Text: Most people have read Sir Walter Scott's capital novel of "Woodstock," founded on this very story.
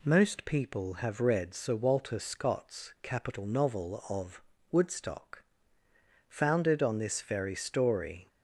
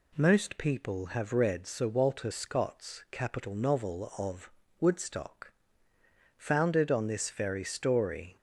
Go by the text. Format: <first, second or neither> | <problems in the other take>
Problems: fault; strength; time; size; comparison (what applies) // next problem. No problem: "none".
neither | pauses between "of" and "Woodstock"; slight; the same in both